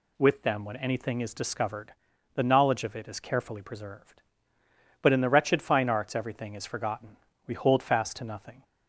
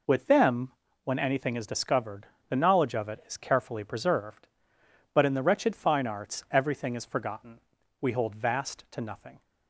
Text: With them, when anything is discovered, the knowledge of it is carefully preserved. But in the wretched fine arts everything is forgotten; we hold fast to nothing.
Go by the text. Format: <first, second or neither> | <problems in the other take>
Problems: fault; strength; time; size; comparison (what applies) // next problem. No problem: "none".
first | says "vast" for "fast"; at 8.3 s